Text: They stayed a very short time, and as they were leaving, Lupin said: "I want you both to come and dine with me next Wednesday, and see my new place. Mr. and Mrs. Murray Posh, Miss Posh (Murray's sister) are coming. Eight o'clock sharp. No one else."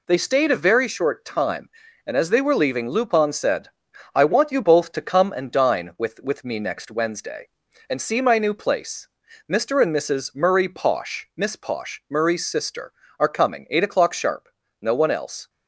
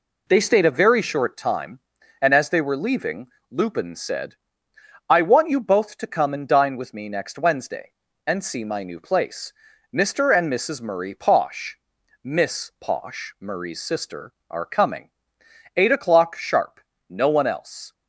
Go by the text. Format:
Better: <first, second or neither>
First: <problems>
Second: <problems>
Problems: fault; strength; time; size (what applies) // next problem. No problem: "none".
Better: second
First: says "with" twice; at 6.2 s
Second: none